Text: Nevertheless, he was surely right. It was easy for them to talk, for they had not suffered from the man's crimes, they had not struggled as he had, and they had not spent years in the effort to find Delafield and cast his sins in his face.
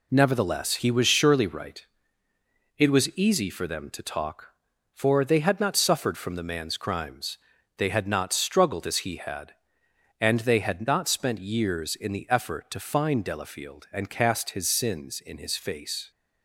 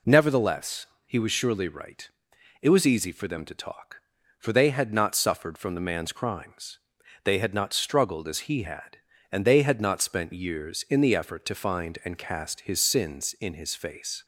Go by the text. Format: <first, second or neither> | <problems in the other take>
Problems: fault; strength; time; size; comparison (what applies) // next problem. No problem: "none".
first | skips "Delafield"; at 12.0 s